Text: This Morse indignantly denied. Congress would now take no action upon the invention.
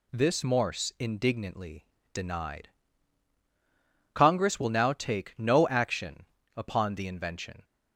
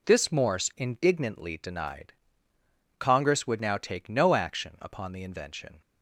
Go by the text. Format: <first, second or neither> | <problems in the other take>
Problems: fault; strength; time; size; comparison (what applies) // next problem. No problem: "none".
second | pauses between "indignantly" and "denied"; slight; at 1.8 s; 0.30 s long // says "will" for "would"; at 4.5 s // pauses between "action" and "upon"; slight; at 6.2 s; 0.30 s long